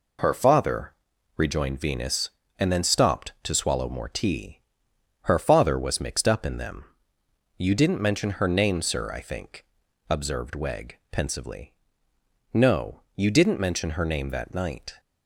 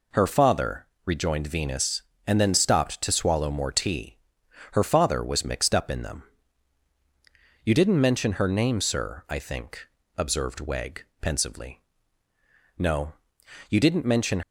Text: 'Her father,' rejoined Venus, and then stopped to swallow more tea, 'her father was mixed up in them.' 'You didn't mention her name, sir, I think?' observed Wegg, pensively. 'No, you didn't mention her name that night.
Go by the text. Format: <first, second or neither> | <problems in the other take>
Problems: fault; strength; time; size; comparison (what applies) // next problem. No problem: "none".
first | stops before "her name that night"; at 14.4 s